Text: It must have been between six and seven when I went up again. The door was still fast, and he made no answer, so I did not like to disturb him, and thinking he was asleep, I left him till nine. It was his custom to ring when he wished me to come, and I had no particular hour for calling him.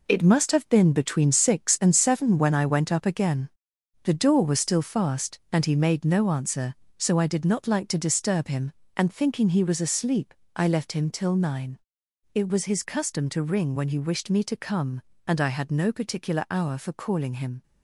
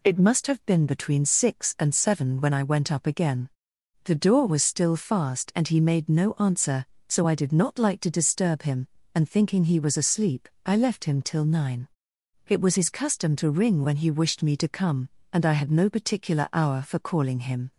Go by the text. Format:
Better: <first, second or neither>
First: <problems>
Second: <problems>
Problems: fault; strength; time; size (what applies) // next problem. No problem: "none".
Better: second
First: gets quieter; strong; throughout; 8 dB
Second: none